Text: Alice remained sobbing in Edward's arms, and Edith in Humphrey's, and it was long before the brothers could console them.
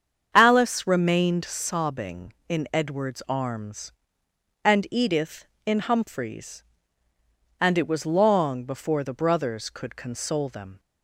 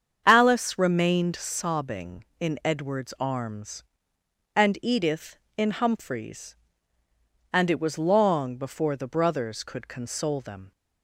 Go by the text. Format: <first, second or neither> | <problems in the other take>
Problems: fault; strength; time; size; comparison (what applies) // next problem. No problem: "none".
neither | starts louder than the rest; strong; the same in both